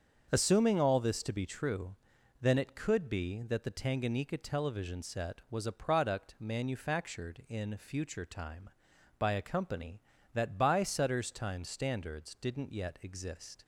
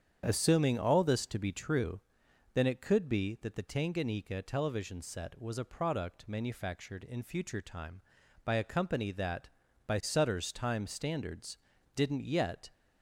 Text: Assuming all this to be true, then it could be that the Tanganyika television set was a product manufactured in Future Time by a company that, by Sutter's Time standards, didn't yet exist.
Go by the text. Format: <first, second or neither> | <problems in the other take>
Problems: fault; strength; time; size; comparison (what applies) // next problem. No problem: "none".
first | starts louder than the rest; strong; until 1.2 s; 8 dB; also in the first // stops before "exist"; at 12.7 s